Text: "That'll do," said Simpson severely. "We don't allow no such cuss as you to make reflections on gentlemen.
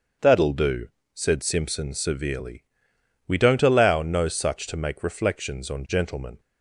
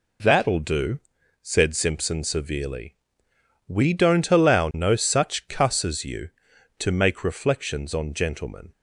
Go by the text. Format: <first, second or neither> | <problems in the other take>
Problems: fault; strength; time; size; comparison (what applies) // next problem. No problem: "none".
second | starts louder than the rest; until 1.4 s; 6.5 dB // skips "cuss as you"; at 4.6 s